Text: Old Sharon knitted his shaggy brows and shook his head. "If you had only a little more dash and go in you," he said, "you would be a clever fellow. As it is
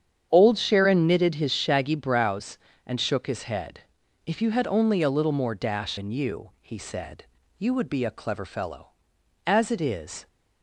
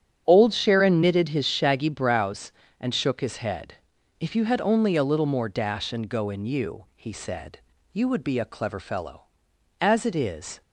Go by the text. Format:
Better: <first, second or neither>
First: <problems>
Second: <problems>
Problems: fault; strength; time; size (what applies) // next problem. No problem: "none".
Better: second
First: starts louder than the rest; strong; until 1.3 s; 8.5 dB // skips "and go"; at 5.9 s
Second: starts louder than the rest; strong; until 1.2 s; 8.5 dB